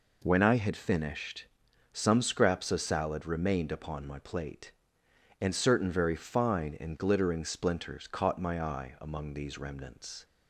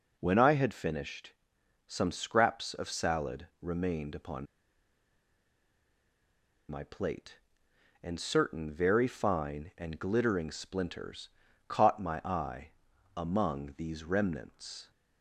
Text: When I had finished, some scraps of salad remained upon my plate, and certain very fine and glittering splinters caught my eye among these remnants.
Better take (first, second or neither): first